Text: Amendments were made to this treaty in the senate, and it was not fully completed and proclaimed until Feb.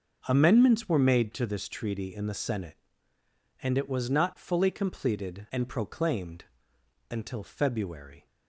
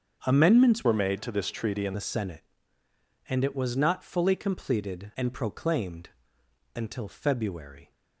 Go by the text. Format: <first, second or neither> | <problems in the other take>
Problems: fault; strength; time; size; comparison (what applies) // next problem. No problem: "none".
first | starts louder than the rest; until 1.2 s; 7 dB; noticeable in the first // changes voice from "were" to "in"; from 0.8 to 1.9 s; 1.1 s long // pauses between "proclaimed" and "until"; noticeable; at 6.0 s; 0.66 s long; noticeable in the first